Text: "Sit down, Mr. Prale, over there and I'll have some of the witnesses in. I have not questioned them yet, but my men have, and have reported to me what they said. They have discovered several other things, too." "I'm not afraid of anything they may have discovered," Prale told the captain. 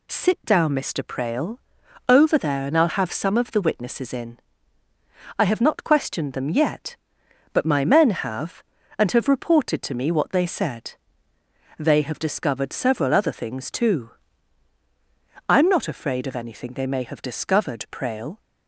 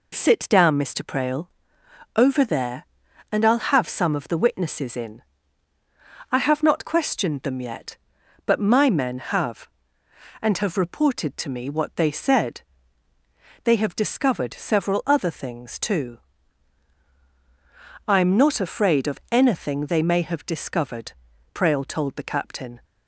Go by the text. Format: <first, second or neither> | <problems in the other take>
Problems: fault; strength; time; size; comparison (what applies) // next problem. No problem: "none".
second | stops before "told the captain"; at 18.3 s